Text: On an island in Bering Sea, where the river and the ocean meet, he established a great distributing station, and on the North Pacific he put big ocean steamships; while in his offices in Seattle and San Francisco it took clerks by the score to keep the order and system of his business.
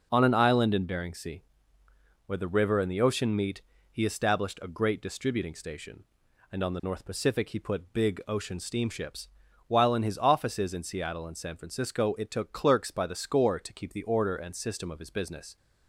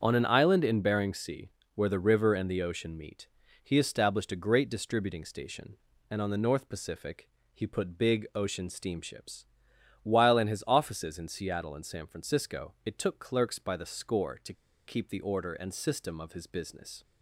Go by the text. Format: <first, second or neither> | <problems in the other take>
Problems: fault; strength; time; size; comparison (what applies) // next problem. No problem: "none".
first | starts louder than the rest; until 1.0 s; 7 dB // pauses between "Pacific" and "he"; slight; at 7.2 s; 0.26 s long // pauses between "to" and "keep"; slight; at 14.5 s; 0.32 s long